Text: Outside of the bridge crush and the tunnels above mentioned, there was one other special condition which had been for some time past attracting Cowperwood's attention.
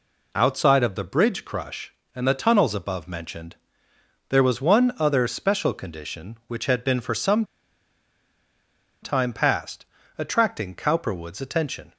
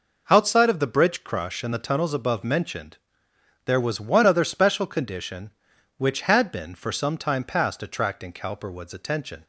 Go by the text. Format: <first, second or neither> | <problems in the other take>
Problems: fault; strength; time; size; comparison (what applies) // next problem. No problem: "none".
second | pauses between "some" and "time"; strong; at 7.4 s; 1.5 s long // pauses between "past" and "attracting"; slight; at 9.8 s; 0.32 s long